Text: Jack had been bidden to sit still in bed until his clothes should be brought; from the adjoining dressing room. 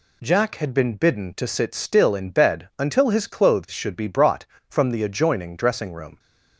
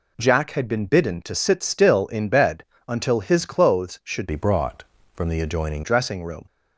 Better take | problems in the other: first | pauses between "bed" and "until"; slight; at 2.6 s; 0.24 s long // changes voice from "be" to "adjoining"; from 4.2 to 5.8 s; 1.6 s long

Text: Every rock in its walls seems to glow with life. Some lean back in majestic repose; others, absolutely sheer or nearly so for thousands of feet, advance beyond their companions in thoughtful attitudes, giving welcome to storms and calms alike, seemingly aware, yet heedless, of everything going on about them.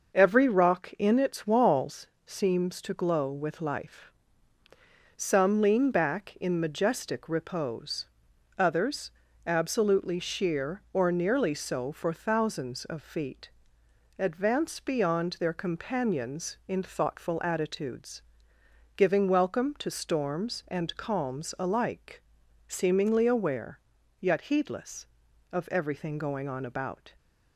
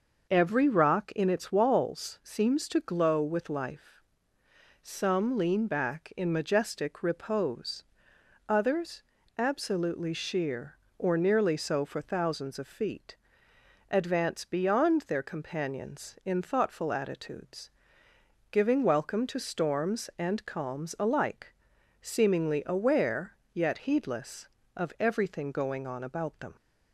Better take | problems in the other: second | pauses between "walls" and "seems"; slight; at 2.0 s; 0.18 s long // stops before "them"; at 27.1 s

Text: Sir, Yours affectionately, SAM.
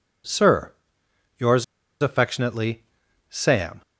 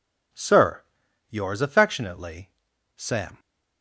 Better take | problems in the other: second | pauses between "Yours" and "affectionately"; at 1.6 s; 0.38 s long

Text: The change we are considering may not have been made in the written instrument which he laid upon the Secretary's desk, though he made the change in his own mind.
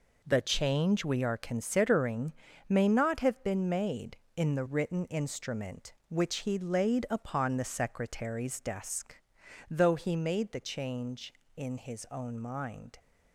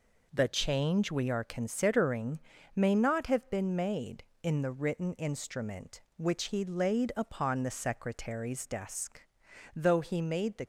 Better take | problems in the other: first | pauses between "considering" and "may"; slight; at 2.3 s; 0.36 s long; slight in the first // stops before "change in his own mind"; at 10.6 s

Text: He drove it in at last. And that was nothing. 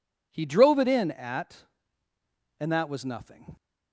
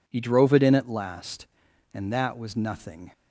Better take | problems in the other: second | skips "last"; at 2.1 s

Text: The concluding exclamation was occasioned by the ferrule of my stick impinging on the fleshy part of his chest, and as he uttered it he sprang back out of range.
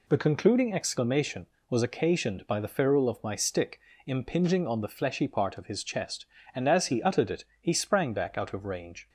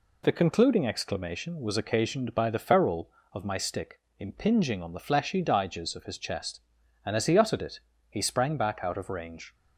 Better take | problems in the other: first | pauses between "stick" and "impinging"; slight; at 4.0 s; 0.18 s long; slight in the first // says "diges" for "part"; at 5.4 s // pauses between "it" and "he"; slight; at 7.8 s; 0.28 s long; slight in the first

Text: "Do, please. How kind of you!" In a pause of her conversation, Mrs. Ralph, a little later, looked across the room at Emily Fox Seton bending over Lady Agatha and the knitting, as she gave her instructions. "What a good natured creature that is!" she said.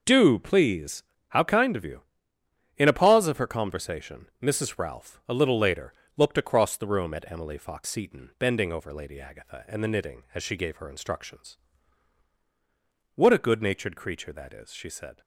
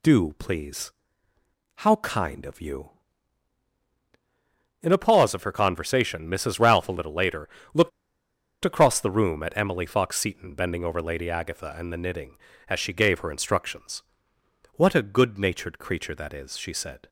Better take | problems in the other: first | pauses between "looked" and "across"; noticeable; at 7.9 s; 0.73 s long

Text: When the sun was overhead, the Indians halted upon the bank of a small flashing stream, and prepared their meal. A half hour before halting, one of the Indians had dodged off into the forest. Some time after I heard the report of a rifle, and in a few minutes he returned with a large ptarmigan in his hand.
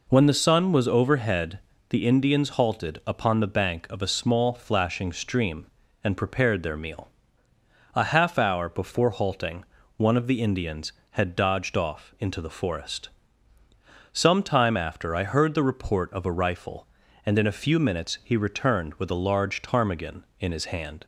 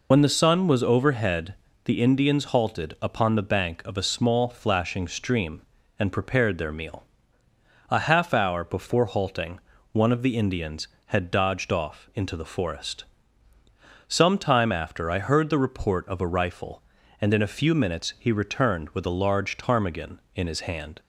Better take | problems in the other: first | loses the start of "When"; at 0.1 s; 65 ms

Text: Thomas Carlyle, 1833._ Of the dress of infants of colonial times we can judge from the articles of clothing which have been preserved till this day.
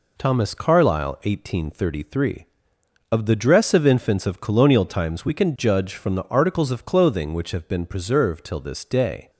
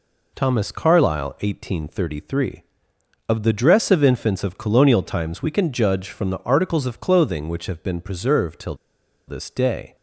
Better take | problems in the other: first | pauses between "till" and "this"; noticeable; at 8.7 s; 0.52 s long

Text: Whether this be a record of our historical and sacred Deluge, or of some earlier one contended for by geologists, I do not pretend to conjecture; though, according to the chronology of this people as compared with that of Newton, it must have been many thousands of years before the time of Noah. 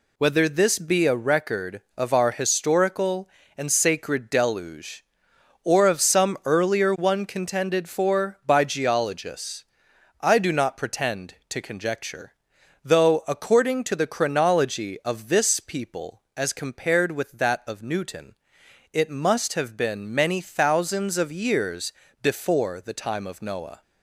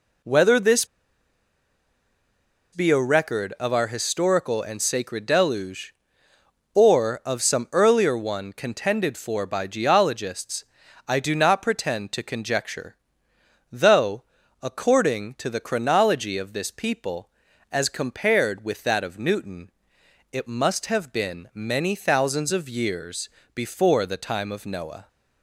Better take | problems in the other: first | pauses between "this" and "be"; strong; at 0.8 s; 1.8 s long // pauses between "years" and "before"; slight; at 23.2 s; 0.26 s long; slight in the first

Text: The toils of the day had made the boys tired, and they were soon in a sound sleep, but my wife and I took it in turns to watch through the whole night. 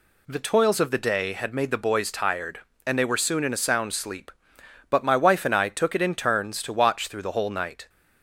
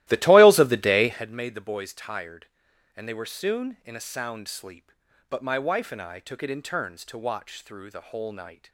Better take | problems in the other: first | starts louder than the rest; strong; until 1.3 s; 16 dB

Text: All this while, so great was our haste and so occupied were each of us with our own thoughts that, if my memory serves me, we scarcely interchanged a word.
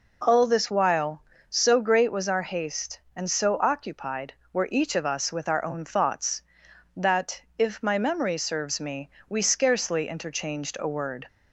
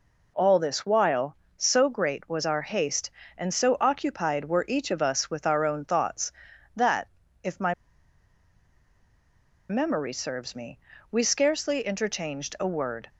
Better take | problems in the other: first | pauses between "my" and "memory"; strong; at 7.7 s; 1.9 s long

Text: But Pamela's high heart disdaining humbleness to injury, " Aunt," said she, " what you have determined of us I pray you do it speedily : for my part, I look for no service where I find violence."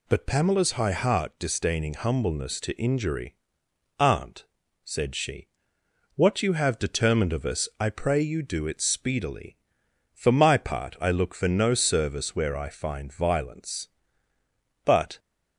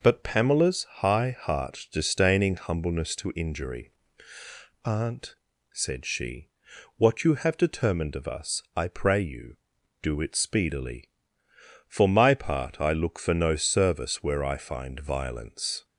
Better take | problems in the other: second | goes on to say "But"; slight; from 14.8 s on; 0.34 s long

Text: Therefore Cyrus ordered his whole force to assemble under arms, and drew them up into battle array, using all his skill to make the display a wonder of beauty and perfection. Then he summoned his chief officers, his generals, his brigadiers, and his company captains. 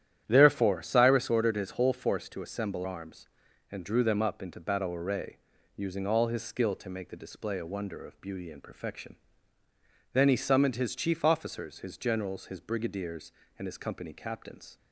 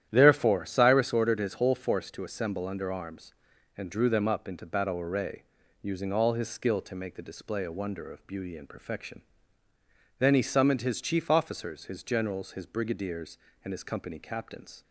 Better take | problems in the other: second | starts louder than the rest; strong; until 1.2 s; 11 dB; strong in the second // skips "under"; at 2.8 s

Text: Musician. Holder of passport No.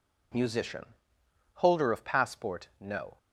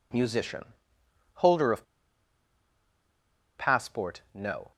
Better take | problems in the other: first | pauses between "of" and "passport"; strong; at 1.8 s; 1.7 s long

